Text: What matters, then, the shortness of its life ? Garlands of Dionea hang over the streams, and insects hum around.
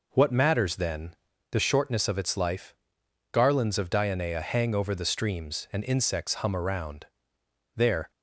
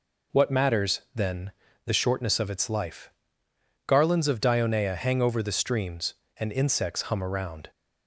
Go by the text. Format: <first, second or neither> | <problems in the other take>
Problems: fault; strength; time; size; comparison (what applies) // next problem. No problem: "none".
second | goes on to say "There"; slight; from 7.7 s on; 0.34 s long